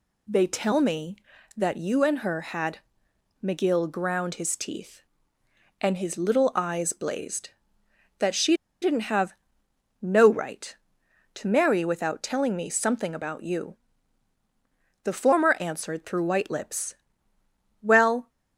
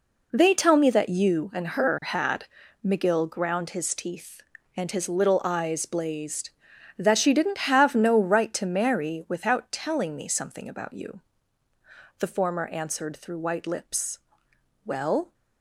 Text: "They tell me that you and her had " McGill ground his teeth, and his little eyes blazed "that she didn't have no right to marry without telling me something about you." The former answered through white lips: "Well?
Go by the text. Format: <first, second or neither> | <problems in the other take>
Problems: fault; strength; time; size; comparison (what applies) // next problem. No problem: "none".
second | pauses between "she" and "didn't"; slight; at 8.5 s; 0.28 s long // pauses between "have" and "no"; noticeable; at 9.3 s; 0.66 s long